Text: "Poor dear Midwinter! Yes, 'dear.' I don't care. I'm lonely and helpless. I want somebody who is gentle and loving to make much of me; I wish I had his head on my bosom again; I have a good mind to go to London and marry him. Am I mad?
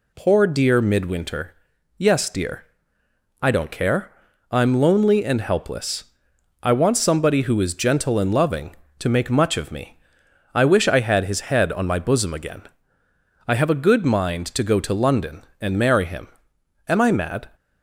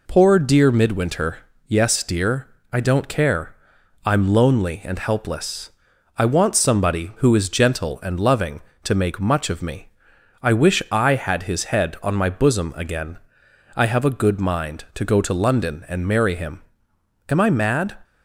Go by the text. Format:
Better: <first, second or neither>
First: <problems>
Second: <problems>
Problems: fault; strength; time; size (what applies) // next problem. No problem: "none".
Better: neither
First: none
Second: none